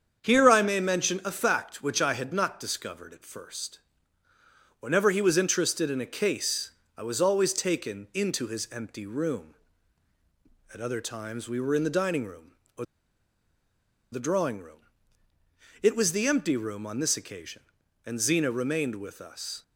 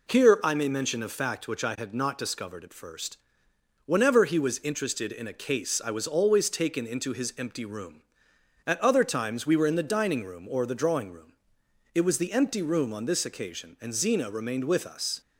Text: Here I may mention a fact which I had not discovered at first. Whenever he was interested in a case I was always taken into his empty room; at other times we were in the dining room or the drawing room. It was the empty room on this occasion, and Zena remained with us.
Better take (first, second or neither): second